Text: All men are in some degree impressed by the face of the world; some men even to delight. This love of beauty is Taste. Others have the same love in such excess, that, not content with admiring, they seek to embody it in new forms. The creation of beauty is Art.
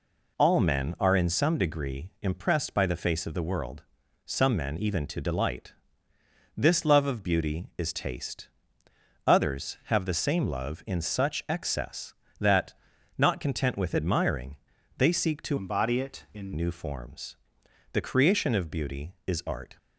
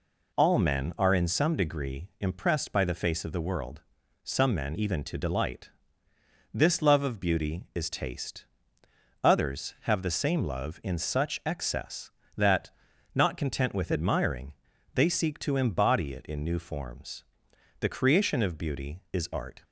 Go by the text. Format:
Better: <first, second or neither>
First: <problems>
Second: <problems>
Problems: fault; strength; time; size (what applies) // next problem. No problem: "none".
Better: second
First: changes voice from "embody" to "in"; from 15.5 to 16.5 s; 1.0 s long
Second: none